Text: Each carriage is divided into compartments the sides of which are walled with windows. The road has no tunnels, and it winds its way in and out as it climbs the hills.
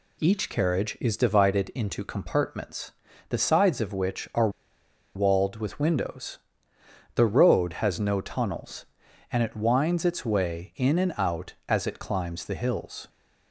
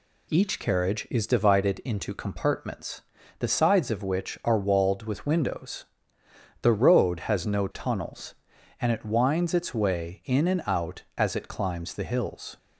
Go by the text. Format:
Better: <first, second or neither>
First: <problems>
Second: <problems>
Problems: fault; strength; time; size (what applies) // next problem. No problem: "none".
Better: second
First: pauses between "compartments" and "the"; at 2.9 s; 0.38 s long // pauses between "are" and "walled"; noticeable; at 4.4 s; 0.66 s long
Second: pauses between "compartments" and "the"; at 3.0 s; 0.38 s long